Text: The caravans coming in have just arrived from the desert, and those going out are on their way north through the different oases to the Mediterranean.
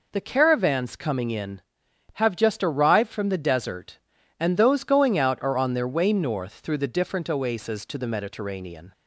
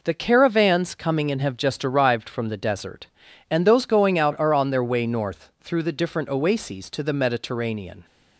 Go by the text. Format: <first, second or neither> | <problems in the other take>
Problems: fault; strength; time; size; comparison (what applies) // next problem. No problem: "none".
neither | none